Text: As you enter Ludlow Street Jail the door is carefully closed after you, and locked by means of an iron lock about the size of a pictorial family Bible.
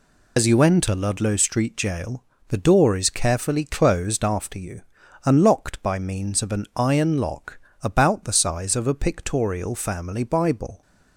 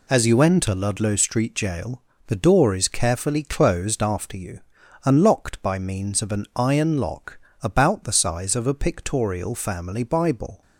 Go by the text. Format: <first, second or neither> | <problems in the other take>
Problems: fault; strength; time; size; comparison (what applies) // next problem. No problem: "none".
second | loses the start of "As"; at 0.3 s; 65 ms // pauses between "Jail" and "the"; slight; at 2.2 s; 0.26 s long; slight in the second // pauses between "lock" and "about"; slight; at 7.5 s; 0.24 s long; slight in the second